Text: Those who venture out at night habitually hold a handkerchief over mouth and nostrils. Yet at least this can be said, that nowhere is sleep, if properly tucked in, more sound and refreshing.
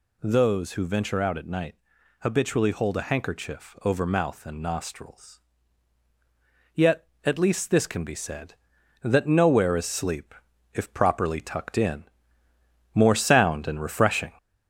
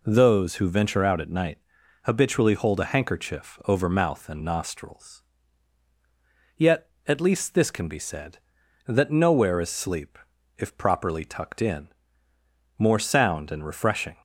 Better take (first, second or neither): second